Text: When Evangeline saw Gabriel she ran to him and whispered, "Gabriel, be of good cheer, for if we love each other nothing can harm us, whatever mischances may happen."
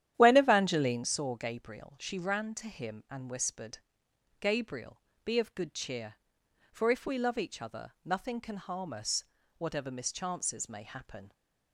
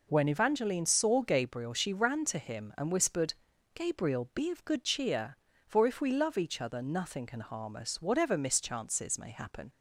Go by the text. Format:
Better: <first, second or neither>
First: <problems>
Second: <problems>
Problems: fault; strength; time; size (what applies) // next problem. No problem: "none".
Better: second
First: starts louder than the rest; strong; until 1.1 s; 11 dB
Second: none